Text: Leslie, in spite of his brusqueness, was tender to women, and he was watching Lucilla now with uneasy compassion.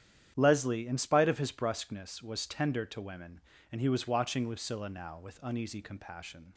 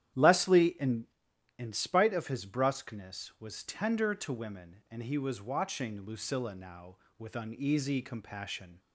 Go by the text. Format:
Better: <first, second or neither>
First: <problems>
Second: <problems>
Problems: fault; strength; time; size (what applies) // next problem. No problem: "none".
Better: first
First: starts louder than the rest; strong; until 1.3 s; 10 dB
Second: starts louder than the rest; strong; until 1.6 s; 11 dB // says "in" twice; at 1.5 s